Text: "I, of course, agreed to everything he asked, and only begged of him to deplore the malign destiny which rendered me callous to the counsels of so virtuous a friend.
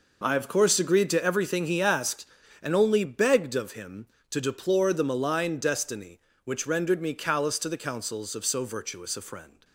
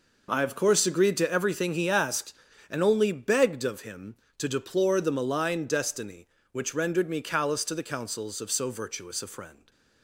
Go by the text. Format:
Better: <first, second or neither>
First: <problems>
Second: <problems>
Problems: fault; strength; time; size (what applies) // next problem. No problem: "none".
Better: neither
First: none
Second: none